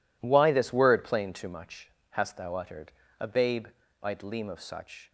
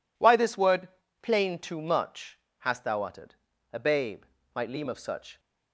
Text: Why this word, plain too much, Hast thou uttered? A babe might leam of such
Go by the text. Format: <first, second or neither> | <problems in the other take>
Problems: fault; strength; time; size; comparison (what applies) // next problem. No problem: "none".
neither | pauses between "babe" and "might"; slight; the same in both